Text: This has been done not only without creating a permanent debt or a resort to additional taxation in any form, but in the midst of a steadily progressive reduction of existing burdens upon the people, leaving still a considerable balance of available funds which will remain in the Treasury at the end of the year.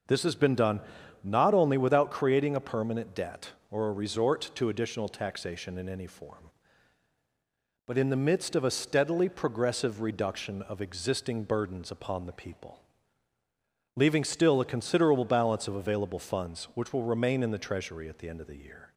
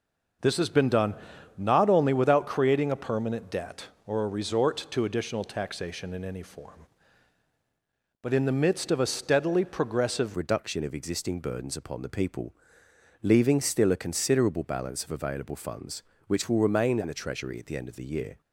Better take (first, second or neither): first